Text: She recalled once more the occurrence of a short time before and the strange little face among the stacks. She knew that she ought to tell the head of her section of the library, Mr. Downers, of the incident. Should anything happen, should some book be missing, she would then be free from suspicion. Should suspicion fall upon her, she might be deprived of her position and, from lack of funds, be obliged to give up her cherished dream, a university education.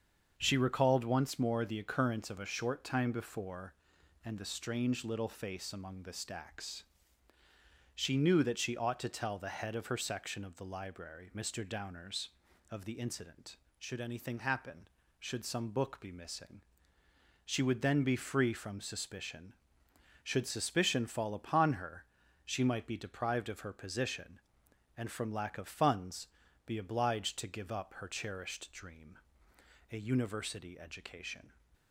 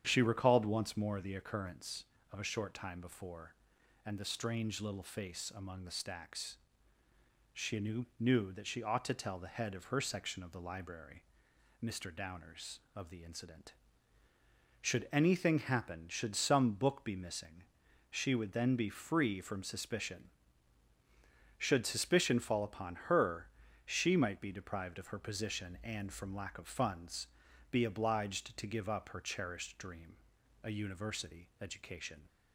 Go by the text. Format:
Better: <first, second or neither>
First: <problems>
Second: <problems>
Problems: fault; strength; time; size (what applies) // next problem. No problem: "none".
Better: first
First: starts louder than the rest; until 1.3 s; 7 dB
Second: starts louder than the rest; strong; until 1.0 s; 9 dB // says "knew" twice; at 8.1 s